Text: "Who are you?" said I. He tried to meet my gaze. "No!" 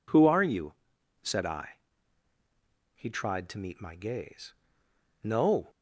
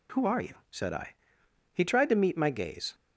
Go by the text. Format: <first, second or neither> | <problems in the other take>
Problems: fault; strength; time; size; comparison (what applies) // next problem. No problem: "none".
first | stops before "No"; at 2.9 s